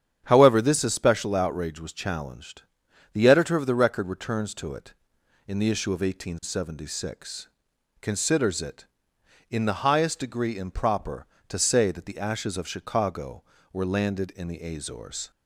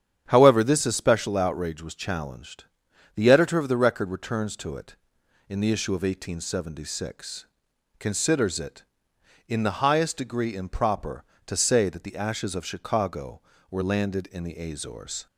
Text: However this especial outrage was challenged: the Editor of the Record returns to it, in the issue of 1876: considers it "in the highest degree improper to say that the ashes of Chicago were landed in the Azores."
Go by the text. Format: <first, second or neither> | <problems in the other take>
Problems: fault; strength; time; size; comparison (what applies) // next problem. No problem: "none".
neither | starts louder than the rest; strong; the same in both